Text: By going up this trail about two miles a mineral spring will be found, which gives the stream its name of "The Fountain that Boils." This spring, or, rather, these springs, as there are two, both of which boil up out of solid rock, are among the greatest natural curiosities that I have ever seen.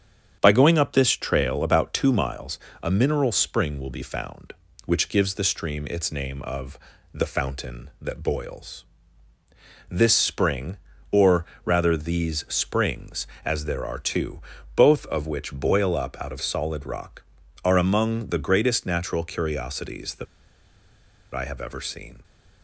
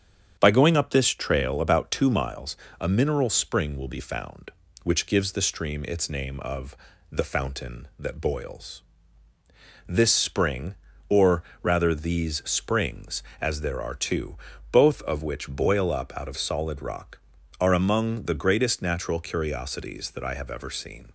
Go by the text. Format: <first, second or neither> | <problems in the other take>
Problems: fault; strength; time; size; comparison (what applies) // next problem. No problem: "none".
second | starts louder than the rest; strong; until 1.4 s; 8 dB; strong in the second // pauses between "miles" and "a"; slight; at 2.5 s; 0.24 s long; slight in the second // pauses between "of" and "The"; slight; at 6.7 s; 0.36 s long; slight in the second // pauses between "that" and "I"; at 20.2 s; 1.0 s long